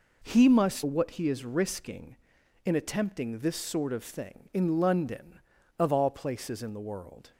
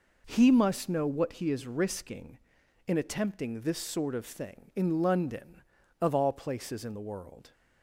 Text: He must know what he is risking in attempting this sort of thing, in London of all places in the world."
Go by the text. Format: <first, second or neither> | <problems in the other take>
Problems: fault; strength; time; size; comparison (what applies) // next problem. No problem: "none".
second | skips "know"; at 0.8 s